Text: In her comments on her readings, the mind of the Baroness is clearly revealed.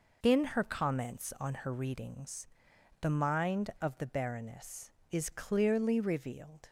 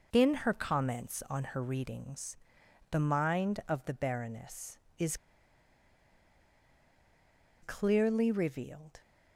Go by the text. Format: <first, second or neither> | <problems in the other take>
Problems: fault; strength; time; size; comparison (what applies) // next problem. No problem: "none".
first | pauses between "is" and "clearly"; strong; at 5.1 s; 2.4 s long